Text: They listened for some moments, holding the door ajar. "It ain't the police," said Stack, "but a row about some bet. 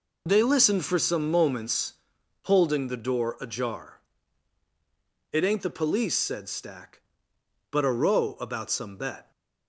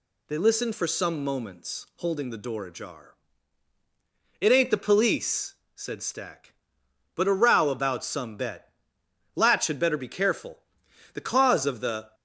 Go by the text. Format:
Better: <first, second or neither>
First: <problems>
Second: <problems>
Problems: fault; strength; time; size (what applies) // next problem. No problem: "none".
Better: first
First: none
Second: goes on to say "Latch had better be careful The cause of the"; strong; from 9.3 s on; 2.7 s long